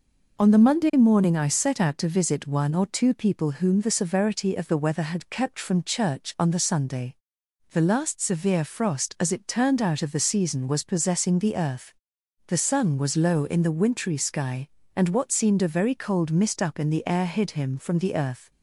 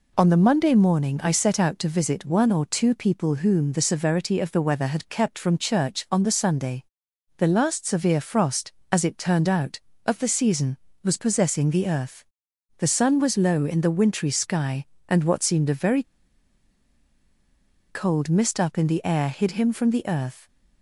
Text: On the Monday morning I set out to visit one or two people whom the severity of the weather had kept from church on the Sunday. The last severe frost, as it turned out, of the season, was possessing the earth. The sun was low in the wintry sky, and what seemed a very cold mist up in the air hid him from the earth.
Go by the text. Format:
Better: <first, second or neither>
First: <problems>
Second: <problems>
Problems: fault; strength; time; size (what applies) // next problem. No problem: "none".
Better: first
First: none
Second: pauses between "very" and "cold"; strong; at 16.0 s; 1.8 s long